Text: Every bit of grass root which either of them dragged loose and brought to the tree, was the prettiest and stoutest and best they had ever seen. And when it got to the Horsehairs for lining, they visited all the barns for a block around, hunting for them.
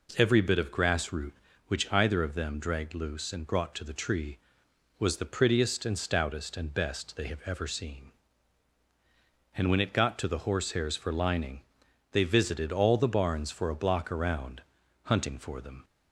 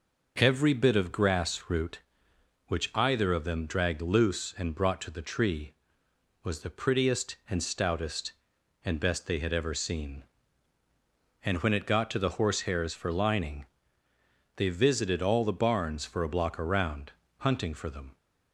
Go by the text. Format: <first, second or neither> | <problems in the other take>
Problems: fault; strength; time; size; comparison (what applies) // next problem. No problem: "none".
second | says "have" for "had"; at 7.2 s